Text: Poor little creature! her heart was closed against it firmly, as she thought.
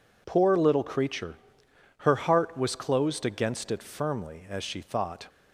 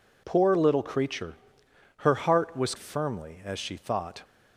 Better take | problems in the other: first | skips "closed against it"; at 2.7 s

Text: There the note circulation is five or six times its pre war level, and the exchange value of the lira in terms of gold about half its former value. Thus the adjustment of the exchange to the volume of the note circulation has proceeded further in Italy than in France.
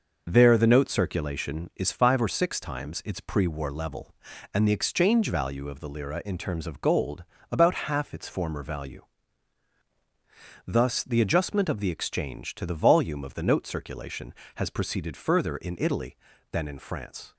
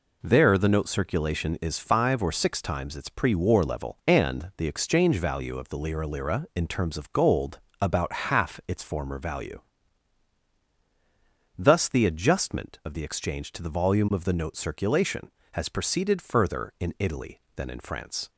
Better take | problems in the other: first | says "lira" twice; at 6.0 s // pauses between "gold" and "about"; slight; at 7.6 s; 0.20 s long; slight in the first

